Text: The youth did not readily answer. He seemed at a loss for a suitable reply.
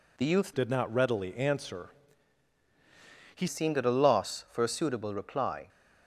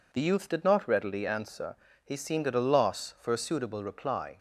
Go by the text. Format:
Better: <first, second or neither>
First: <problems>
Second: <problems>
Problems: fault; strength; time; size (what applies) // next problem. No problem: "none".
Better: second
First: changes voice from "did" to "He"; from 0.5 to 3.4 s; 2.9 s long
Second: none